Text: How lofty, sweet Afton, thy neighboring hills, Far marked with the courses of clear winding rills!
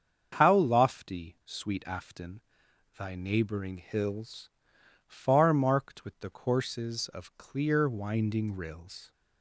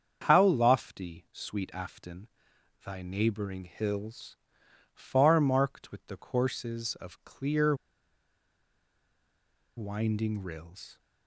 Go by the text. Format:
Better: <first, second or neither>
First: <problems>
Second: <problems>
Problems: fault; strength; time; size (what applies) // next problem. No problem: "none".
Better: first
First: starts louder than the rest; strong; until 1.4 s; 7 dB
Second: starts louder than the rest; strong; until 1.3 s; 7 dB // pauses between "clear" and "winding"; strong; at 7.7 s; 2.0 s long